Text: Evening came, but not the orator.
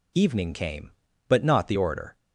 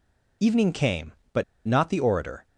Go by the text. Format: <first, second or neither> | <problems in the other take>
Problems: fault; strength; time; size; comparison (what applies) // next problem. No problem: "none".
first | pauses between "but" and "not"; slight; at 1.4 s; 0.24 s long